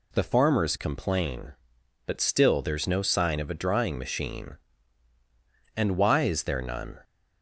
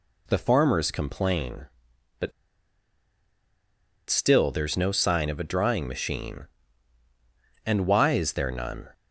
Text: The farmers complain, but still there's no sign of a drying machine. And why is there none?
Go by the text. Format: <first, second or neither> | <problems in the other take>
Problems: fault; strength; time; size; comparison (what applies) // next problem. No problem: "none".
first | pauses between "but" and "still"; strong; at 2.3 s; 1.7 s long